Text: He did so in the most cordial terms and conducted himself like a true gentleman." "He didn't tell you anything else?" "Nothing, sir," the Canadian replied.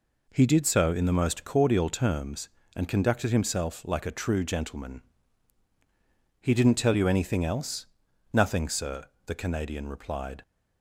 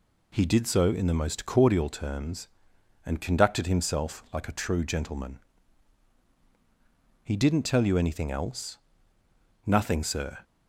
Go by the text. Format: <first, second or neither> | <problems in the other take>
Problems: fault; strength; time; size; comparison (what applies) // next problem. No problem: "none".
first | stops before "the Canadian replied"; at 10.4 s